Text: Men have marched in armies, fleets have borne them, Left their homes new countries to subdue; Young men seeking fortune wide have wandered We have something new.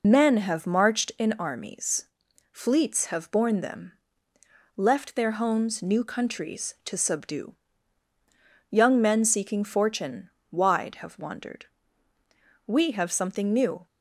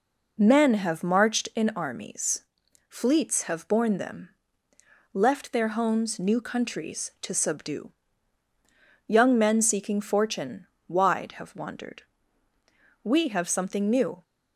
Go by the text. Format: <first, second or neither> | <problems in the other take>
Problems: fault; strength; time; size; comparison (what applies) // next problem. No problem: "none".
second | loses the start of "Men"; at 0.0 s; 35 ms // pauses between "fortune" and "wide"; slight; at 10.3 s; 0.18 s long; slight in the second // pauses between "wandered" and "We"; at 11.6 s; 1.0 s long; also in the second